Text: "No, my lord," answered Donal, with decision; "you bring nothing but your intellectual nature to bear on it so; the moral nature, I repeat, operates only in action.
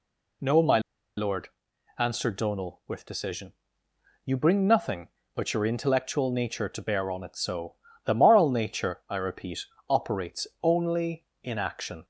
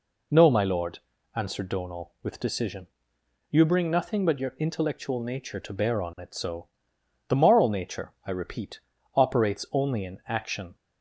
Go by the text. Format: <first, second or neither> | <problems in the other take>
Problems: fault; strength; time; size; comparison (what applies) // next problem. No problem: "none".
second | pauses between "my" and "lord"; at 0.7 s; 0.37 s long // pauses between "operates" and "only"; slight; at 10.4 s; 0.16 s long